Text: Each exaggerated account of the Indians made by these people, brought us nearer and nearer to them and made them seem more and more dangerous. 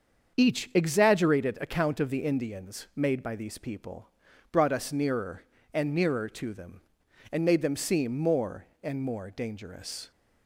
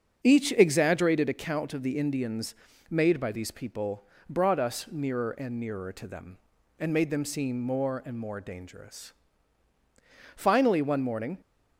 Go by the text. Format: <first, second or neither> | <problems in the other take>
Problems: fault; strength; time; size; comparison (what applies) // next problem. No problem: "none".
first | starts louder than the rest; strong; until 1.2 s; 7.5 dB; also in the first // pauses between "Indians" and "made"; slight; at 2.5 s; 0.36 s long // goes on to say "Finally one morning"; noticeable; from 10.3 s on; 1.0 s long